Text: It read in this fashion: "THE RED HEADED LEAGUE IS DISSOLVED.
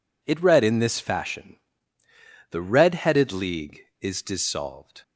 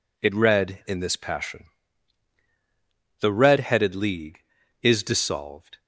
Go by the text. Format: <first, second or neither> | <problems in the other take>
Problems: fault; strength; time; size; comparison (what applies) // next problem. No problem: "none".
first | says "passion" for "fashion"; at 1.1 s